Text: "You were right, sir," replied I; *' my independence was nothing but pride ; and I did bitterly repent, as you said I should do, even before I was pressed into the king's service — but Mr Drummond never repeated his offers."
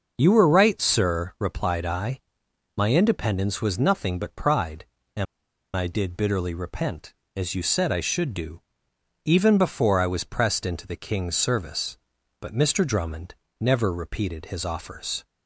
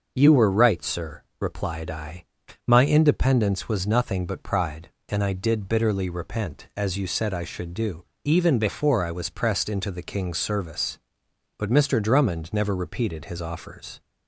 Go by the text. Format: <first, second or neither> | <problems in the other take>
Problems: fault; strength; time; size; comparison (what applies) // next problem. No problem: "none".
second | starts louder than the rest; noticeable; until 1.1 s; 6 dB // pauses between "and" and "I"; noticeable; at 5.2 s; 0.50 s long // pauses between "Drummond" and "never"; slight; at 13.3 s; 0.26 s long